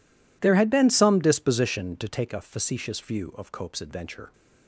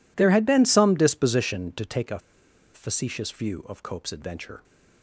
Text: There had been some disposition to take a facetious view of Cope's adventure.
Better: first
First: none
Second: pauses between "a" and "facetious"; noticeable; at 2.2 s; 0.54 s long

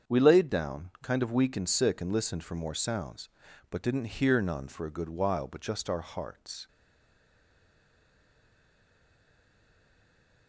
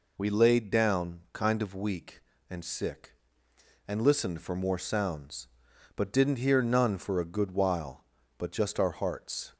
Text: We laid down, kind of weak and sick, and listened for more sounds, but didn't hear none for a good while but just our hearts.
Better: second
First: starts louder than the rest; strong; until 1.1 s; 7.5 dB // stays silent after the last word; strong; from 6.6 s on; 3.8 s long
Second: none

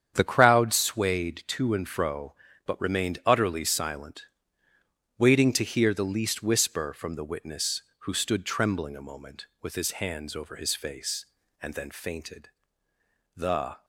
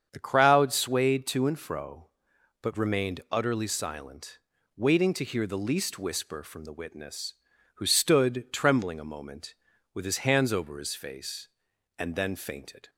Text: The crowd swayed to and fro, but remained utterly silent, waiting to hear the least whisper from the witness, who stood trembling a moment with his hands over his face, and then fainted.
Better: second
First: starts louder than the rest; strong; until 1.1 s; 8 dB // goes on to say "The"; from 13.3 s on; 0.50 s long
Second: starts louder than the rest; strong; until 1.1 s; 7.5 dB

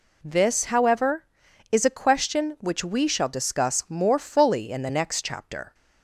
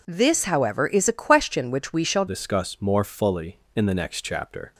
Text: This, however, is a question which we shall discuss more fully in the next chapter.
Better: first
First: none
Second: changes voice at "discuss"; from 2.2 s on; 2.5 s long

